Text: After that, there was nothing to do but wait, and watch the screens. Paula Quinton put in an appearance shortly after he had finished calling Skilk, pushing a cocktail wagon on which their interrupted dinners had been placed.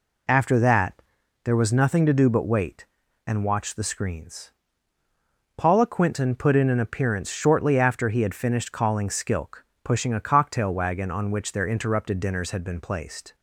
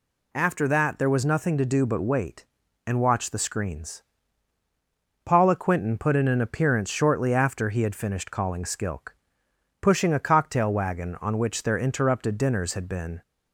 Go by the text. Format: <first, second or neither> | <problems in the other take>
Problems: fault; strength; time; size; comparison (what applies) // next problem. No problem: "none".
first | stops before "placed"; at 13.2 s